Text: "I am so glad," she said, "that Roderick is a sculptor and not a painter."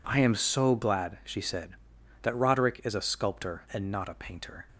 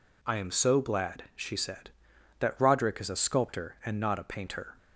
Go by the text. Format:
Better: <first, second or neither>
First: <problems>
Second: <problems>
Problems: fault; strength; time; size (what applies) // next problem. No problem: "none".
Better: neither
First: none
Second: none